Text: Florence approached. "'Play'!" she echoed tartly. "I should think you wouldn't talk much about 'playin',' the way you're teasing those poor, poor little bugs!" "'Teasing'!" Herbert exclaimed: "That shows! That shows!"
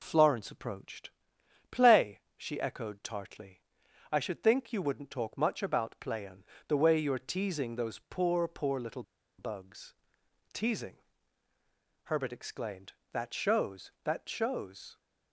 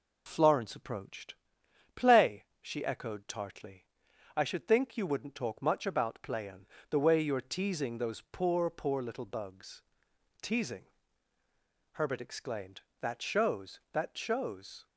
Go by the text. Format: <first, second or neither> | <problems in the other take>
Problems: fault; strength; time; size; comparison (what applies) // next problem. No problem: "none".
second | pauses between "little" and "bugs"; slight; at 9.0 s; 0.33 s long